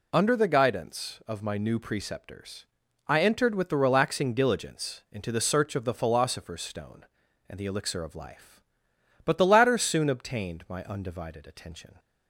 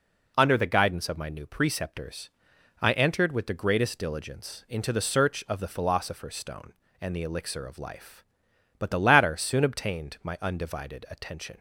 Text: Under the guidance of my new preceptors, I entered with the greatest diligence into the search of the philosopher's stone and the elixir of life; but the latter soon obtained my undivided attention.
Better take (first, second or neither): second